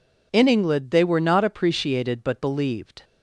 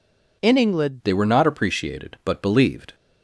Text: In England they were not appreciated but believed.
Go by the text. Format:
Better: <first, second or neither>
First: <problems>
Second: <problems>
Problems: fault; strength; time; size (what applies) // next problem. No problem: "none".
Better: first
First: none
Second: changes voice at "they"; from 1.0 s on; 1.9 s long